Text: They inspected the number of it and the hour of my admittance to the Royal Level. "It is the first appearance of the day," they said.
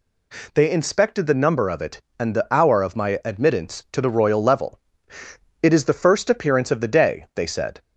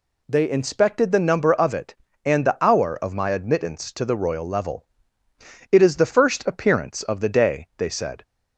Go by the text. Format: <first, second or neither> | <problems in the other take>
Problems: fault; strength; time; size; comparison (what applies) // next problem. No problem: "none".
neither | none